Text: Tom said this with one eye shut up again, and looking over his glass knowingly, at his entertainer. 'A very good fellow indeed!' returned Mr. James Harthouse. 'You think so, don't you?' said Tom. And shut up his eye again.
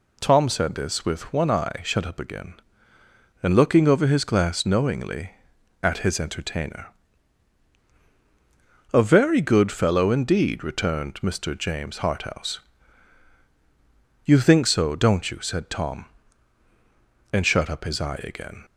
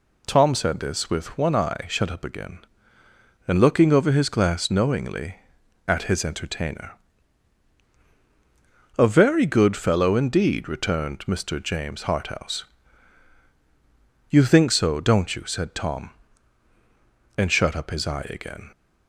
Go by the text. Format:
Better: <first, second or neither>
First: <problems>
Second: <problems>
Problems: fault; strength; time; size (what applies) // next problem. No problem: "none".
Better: neither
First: none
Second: none